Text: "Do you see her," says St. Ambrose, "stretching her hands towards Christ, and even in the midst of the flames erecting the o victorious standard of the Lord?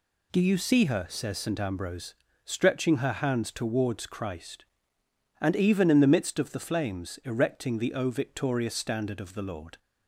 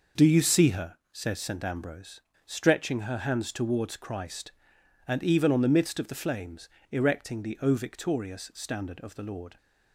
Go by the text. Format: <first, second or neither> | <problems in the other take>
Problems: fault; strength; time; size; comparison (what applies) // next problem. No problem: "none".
first | says "on" for "in"; at 5.5 s // pauses between "flames" and "erecting"; slight; at 6.7 s; 0.20 s long